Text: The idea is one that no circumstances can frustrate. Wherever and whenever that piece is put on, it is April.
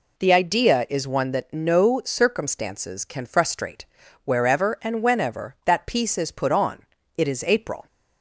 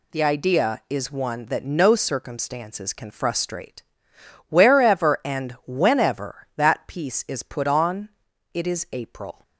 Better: first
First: none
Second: gets quieter; throughout; 7 dB

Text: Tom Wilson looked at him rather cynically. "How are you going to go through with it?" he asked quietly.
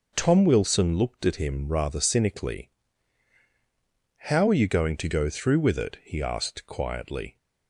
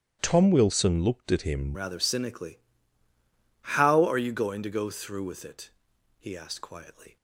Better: first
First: none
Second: starts louder than the rest; strong; until 1.2 s; 10.5 dB // changes voice at "rather"; from 1.7 s on; 5.4 s long

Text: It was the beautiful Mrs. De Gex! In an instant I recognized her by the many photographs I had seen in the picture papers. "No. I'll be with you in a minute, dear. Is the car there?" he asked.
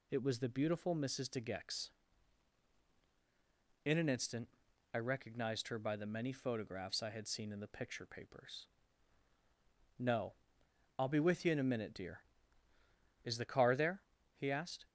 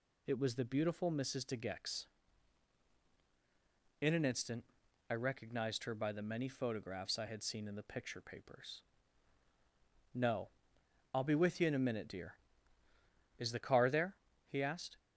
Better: neither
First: pauses between "instant" and "I"; noticeable; at 4.4 s; 0.46 s long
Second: pauses between "instant" and "I"; noticeable; at 4.6 s; 0.46 s long

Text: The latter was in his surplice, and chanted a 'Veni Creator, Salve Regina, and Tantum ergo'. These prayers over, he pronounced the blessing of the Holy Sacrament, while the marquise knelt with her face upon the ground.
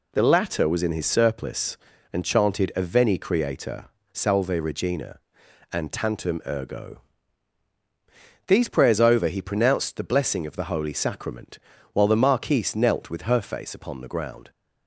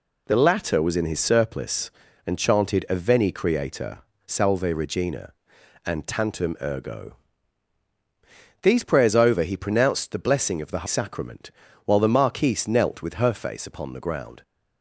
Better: first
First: none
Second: skips "Holy"; at 10.8 s

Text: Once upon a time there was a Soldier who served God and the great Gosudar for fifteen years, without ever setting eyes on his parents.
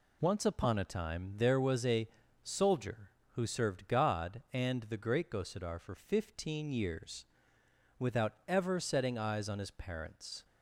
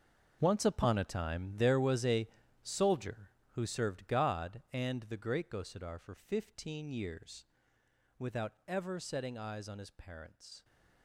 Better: first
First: pauses between "a" and "Soldier"; slight; at 2.0 s; 0.34 s long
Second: gets quieter; strong; throughout; 14 dB // pauses between "a" and "Soldier"; slight; at 2.2 s; 0.34 s long

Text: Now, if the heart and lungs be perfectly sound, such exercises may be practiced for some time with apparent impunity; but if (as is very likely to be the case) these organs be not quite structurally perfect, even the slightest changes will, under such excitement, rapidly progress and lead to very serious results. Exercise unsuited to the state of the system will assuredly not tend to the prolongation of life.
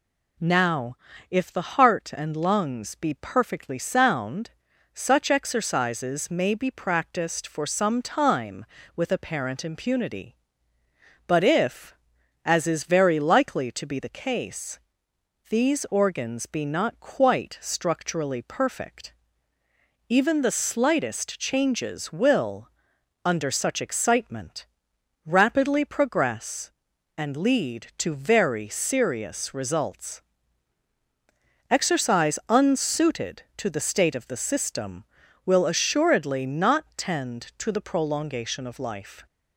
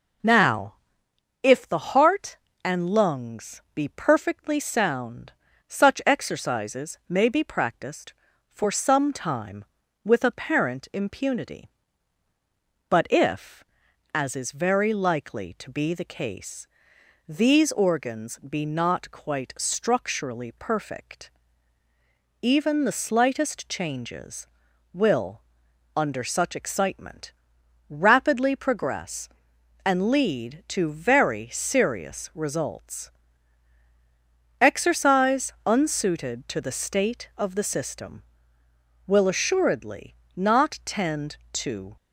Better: first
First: none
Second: pauses between "assuredly" and "not"; slight; at 40.1 s; 0.20 s long // stops before "the prolongation of life"; at 41.9 s

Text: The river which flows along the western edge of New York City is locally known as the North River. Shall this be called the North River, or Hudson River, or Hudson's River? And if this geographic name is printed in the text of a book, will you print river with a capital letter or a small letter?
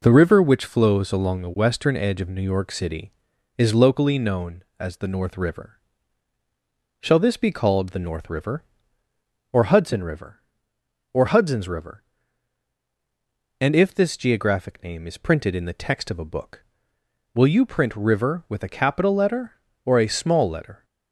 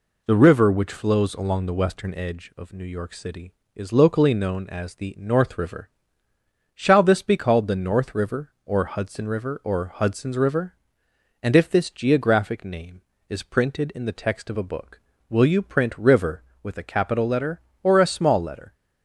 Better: neither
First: none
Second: none

